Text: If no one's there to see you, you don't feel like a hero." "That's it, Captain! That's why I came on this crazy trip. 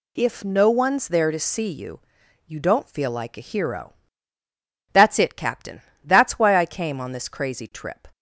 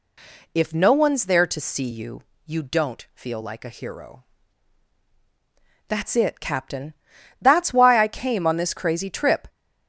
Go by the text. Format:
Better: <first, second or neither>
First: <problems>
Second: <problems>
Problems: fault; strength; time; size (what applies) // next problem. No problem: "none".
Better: neither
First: none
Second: none